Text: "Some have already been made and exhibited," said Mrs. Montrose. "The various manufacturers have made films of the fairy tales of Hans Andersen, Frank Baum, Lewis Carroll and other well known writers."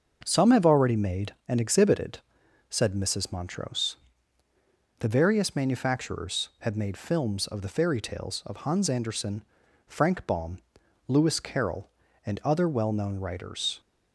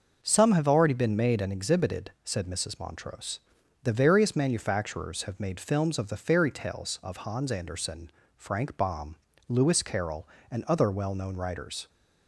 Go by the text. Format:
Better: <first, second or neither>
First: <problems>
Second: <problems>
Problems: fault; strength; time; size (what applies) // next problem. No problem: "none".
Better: second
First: starts louder than the rest; until 1.2 s; 6.5 dB // skips "been"; at 0.9 s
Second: starts louder than the rest; noticeable; until 1.2 s; 6 dB